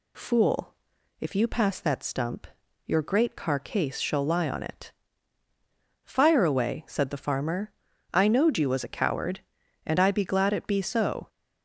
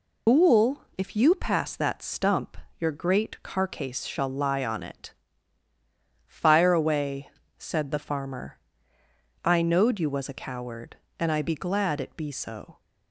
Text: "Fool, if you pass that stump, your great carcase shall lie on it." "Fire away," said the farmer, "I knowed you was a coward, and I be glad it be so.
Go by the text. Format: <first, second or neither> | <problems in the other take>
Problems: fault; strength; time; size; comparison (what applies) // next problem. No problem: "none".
first | loses the start of "Fool"; at 0.2 s; 90 ms